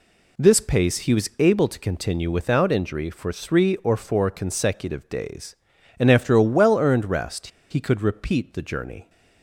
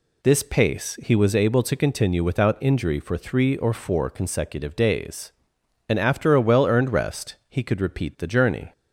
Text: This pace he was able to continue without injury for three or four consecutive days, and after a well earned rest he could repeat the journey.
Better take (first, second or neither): second